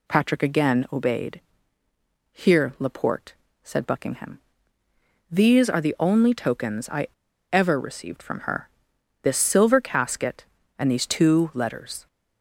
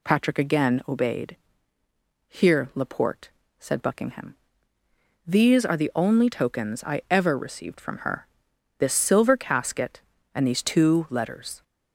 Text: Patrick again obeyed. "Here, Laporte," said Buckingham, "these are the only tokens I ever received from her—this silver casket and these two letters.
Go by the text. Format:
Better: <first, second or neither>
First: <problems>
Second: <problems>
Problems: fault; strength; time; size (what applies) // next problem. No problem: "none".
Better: second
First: pauses between "I" and "ever"; at 7.0 s; 0.44 s long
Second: none